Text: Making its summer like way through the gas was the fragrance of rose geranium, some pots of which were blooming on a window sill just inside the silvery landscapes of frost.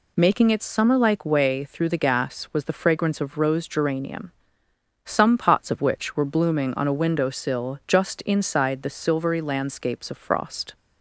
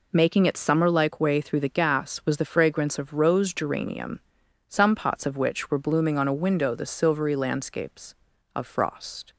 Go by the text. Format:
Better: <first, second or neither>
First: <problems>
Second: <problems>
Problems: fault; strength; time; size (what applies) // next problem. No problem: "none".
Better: first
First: none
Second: skips "sill just inside"; at 6.7 s